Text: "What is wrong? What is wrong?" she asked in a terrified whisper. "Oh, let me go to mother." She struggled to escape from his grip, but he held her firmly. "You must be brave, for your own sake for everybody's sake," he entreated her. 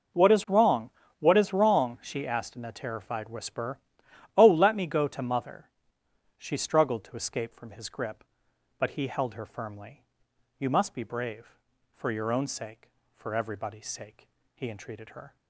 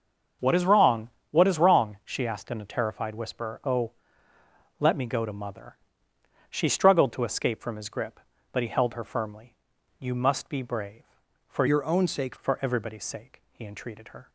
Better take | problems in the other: first | starts louder than the rest; until 1.6 s; 6.5 dB // changes voice from "your" to "sake"; from 11.6 to 12.3 s; 0.7 s long

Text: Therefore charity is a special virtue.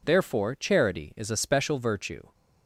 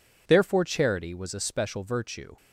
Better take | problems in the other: first | says "was" for "is"; at 1.1 s

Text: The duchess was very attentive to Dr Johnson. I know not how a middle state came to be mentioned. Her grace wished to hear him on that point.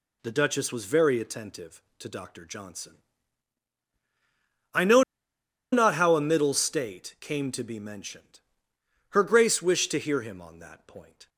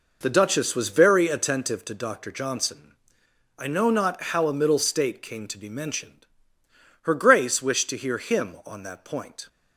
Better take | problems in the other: second | pauses between "know" and "not"; noticeable; at 5.0 s; 0.70 s long

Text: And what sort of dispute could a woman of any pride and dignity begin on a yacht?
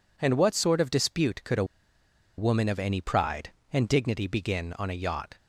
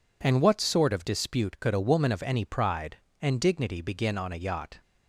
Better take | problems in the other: second | pauses between "a" and "woman"; noticeable; at 1.6 s; 0.73 s long

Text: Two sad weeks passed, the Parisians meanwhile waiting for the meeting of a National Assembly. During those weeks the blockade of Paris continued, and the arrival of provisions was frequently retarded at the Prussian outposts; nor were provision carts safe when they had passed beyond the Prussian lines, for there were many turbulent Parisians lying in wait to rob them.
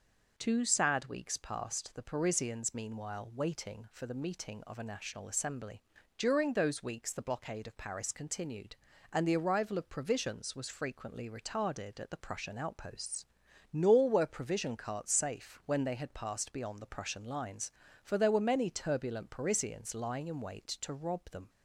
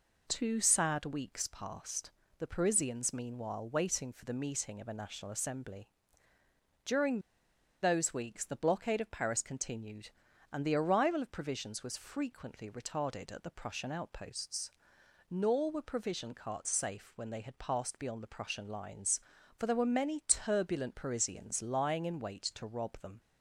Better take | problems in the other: first | pauses between "During" and "those"; noticeable; at 7.2 s; 0.61 s long

